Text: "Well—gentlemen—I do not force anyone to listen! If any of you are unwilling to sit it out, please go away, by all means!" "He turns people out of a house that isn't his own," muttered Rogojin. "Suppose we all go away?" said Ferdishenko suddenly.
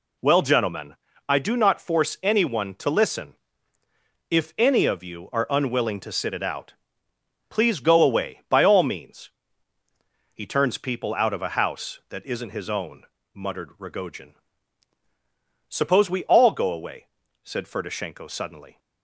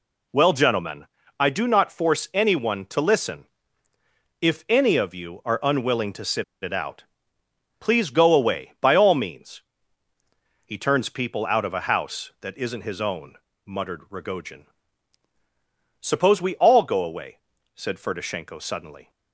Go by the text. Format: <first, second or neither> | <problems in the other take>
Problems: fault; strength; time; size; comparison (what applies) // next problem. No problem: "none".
first | pauses between "sit" and "it"; slight; at 6.4 s; 0.17 s long